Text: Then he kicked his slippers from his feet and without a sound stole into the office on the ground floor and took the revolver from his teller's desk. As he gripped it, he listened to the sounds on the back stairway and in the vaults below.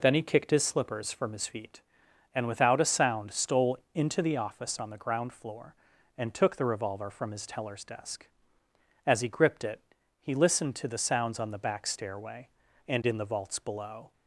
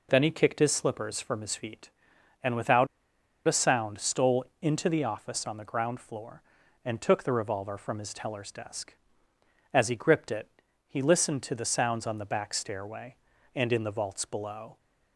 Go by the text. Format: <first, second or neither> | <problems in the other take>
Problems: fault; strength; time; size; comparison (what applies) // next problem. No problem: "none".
first | pauses between "without" and "a"; noticeable; at 2.8 s; 0.61 s long // pauses between "stole" and "into"; slight; at 4.4 s; 0.16 s long; slight in the first